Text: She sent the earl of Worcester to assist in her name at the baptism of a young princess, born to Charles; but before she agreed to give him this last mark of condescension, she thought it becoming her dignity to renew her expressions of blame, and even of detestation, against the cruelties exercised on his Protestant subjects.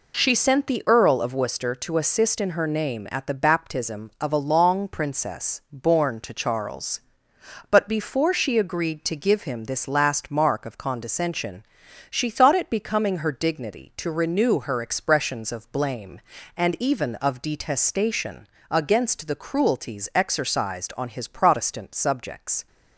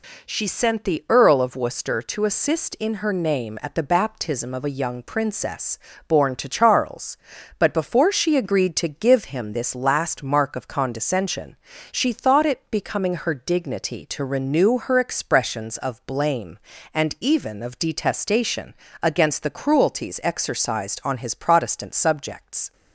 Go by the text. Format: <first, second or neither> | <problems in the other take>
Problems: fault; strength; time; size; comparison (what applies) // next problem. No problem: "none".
second | says "long" for "young"; at 4.4 s